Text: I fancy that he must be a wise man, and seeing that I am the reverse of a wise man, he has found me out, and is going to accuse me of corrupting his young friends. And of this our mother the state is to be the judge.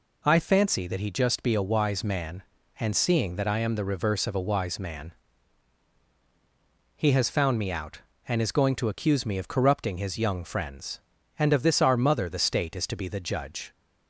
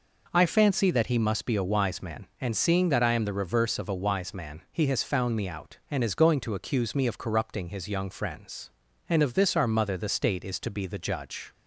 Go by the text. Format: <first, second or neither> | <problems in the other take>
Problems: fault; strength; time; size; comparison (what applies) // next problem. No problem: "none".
second | says "just" for "must"; at 1.1 s